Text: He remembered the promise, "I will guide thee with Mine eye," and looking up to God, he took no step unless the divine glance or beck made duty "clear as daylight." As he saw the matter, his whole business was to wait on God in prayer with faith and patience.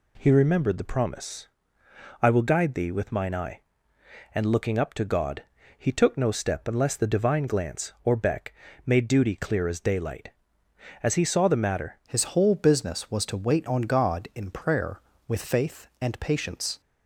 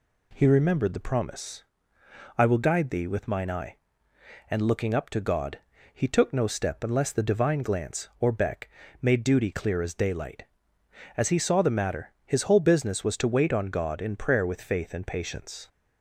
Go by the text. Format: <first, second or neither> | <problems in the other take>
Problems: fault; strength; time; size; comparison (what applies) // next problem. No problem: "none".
second | pauses between "beck" and "made"; slight; at 8.5 s; 0.32 s long; slight in the second // changes voice at "his"; from 12.0 s on; 4.8 s long